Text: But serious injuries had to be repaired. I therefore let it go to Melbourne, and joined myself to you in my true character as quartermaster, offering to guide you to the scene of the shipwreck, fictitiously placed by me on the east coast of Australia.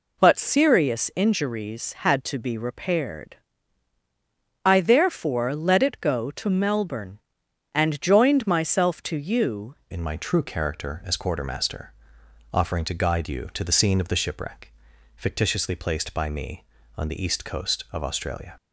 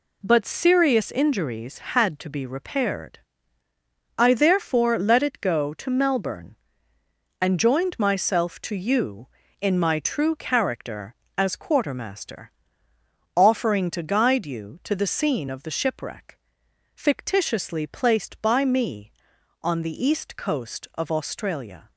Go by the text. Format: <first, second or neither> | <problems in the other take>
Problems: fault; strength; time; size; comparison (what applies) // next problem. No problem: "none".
second | changes voice at "in"; from 9.9 s on; 8.6 s long